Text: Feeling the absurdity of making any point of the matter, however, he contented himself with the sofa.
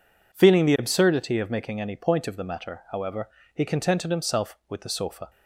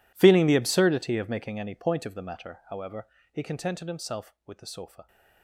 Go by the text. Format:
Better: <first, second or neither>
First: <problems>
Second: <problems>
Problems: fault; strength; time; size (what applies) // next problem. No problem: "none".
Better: first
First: none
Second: gets quieter; strong; throughout; 20 dB